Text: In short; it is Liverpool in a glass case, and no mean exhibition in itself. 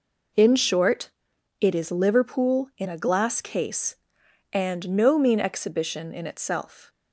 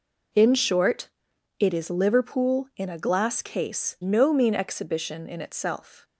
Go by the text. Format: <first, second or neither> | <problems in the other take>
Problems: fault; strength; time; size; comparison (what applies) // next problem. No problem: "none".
first | skips "and"; at 3.9 s